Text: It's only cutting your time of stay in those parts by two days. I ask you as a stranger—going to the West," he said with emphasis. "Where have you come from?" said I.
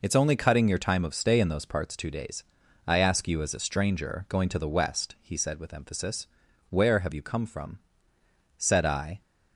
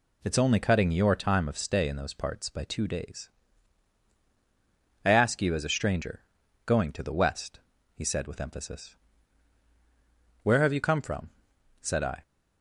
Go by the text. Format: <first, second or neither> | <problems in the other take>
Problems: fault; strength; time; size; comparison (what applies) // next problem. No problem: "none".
second | skips "by"; at 1.9 s